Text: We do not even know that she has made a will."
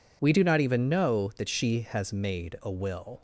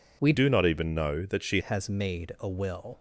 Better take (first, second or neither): first